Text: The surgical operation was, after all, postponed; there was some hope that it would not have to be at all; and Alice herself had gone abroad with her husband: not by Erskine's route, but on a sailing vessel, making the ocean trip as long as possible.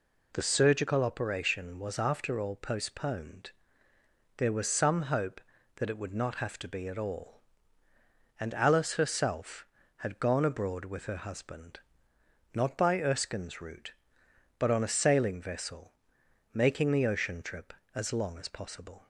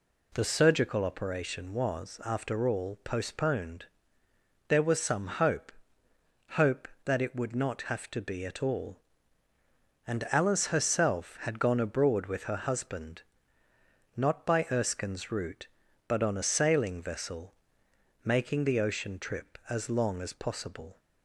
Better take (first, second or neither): first